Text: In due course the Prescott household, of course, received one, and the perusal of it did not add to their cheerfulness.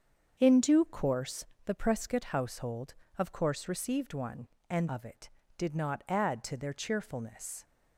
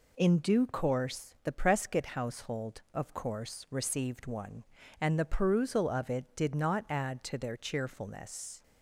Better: second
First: starts louder than the rest; strong; until 1.4 s; 7 dB // pauses between "course" and "the"; slight; at 1.4 s; 0.20 s long // skips "the perusal"; at 4.8 s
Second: none

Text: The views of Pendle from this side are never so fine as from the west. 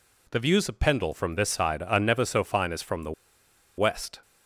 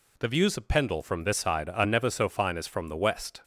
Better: second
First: pauses between "the" and "west"; noticeable; at 3.1 s; 0.65 s long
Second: none

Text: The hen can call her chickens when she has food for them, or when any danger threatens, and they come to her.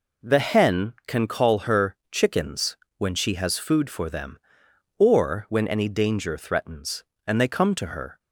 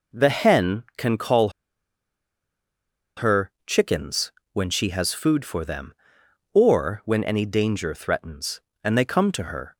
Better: first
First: pauses between "her" and "chickens"; slight; at 1.9 s; 0.16 s long // pauses between "chickens" and "when"; slight; at 2.7 s; 0.22 s long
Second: pauses between "call" and "her"; strong; at 1.4 s; 1.6 s long // pauses between "her" and "chickens"; slight; at 3.5 s; 0.16 s long // pauses between "chickens" and "when"; slight; at 4.3 s; 0.22 s long

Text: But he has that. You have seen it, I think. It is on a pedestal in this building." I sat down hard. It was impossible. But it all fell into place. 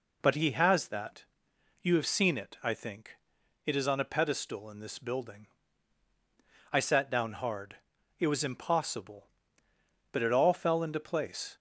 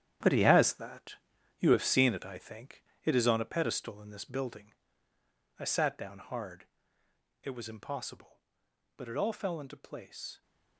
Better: first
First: none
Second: gets quieter; strong; throughout; 10 dB

